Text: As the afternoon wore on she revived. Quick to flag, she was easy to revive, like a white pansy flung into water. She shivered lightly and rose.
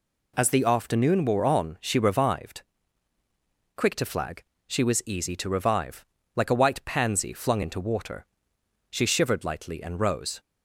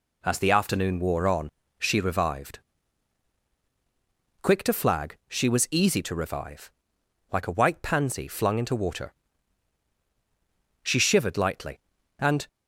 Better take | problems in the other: first | pauses between "on" and "she"; slight; at 1.4 s; 0.32 s long // stops before "rose"; at 12.4 s

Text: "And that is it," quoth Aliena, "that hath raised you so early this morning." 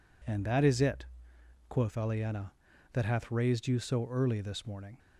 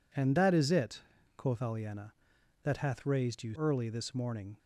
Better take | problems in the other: first | skips "so"; at 3.5 s

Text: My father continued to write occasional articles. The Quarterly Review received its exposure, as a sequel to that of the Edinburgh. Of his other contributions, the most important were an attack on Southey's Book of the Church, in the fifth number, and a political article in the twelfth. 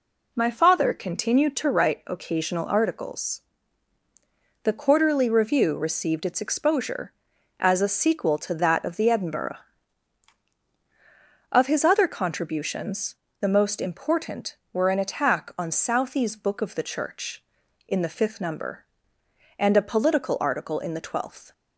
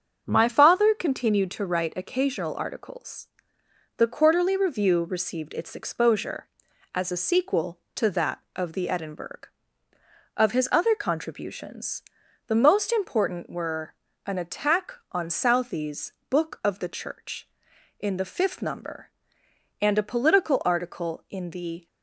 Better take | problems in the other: first | starts louder than the rest; until 1.2 s; 6.5 dB // pauses between "were" and "an"; slight; at 13.9 s; 0.32 s long // pauses between "Southey's" and "Book"; slight; at 16.1 s; 0.18 s long // stops before "twelfth"; at 21.8 s

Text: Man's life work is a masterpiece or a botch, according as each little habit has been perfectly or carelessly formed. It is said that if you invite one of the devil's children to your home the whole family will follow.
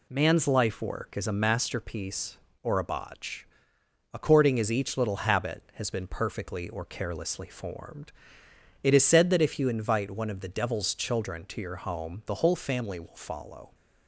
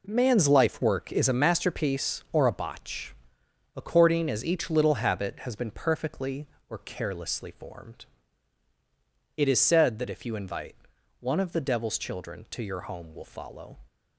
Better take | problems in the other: first | pauses between "invite" and "one"; noticeable; at 10.7 s; 0.46 s long // skips "the whole family"; at 13.1 s

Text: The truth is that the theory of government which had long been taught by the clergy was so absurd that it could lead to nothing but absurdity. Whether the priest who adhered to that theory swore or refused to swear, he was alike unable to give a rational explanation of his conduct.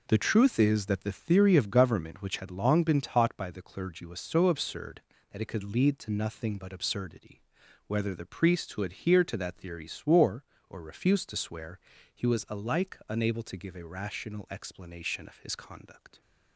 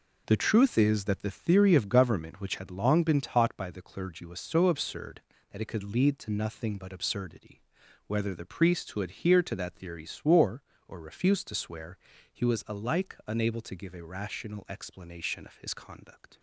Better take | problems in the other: neither | none

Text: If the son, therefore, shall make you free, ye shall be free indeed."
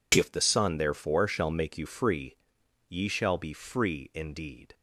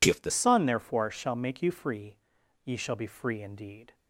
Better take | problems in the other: first | changes voice at "son"; from 0.3 s on; 3.6 s long

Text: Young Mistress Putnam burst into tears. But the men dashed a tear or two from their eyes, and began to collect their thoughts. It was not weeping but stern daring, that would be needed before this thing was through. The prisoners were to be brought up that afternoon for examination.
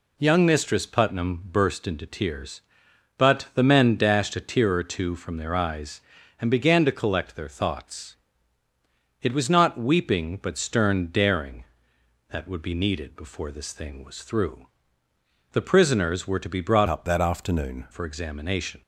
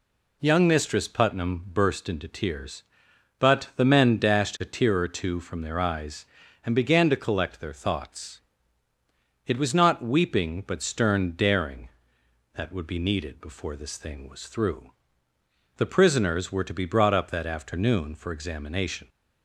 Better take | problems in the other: second | changes voice from "up" to "afternoon"; from 16.8 to 17.8 s; 1.0 s long

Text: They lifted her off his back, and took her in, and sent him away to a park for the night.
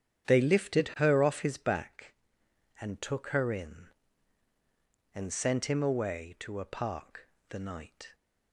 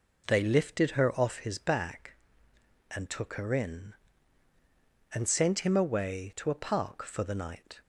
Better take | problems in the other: second | starts louder than the rest; strong; until 1.3 s; 9 dB // skips "for"; at 7.3 s

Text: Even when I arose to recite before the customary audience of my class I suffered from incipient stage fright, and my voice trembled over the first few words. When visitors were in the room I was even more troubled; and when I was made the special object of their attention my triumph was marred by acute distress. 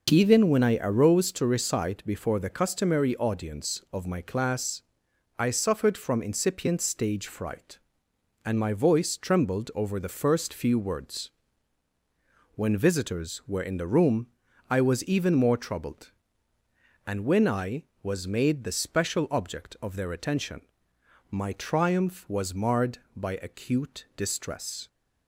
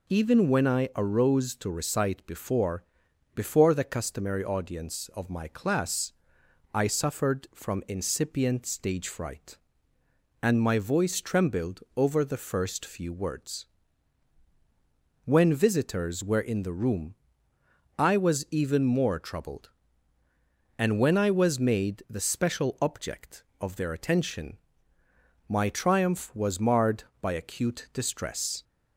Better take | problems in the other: first | says "before" twice; at 3.3 s // pauses between "class" and "I"; noticeable; at 6.1 s; 0.64 s long; noticeable in the first // pauses between "room" and "I"; noticeable; at 17.1 s; 0.82 s long; also in the first // pauses between "attention" and "my"; noticeable; at 24.5 s; 0.90 s long; noticeable in the first

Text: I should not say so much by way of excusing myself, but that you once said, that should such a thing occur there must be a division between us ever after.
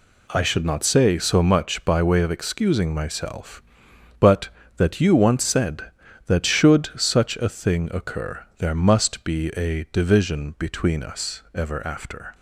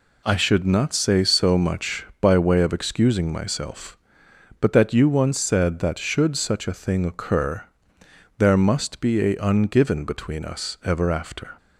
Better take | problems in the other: first | pauses between "occur" and "there"; noticeable; at 7.6 s; 0.76 s long // says "ungiven" for "division"; at 9.3 s

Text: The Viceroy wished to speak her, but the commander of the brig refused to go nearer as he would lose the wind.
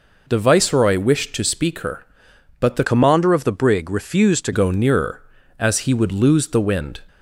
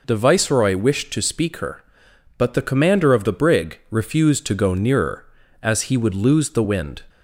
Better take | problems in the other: second | changes voice from "commander" to "to"; from 2.8 to 4.5 s; 1.7 s long

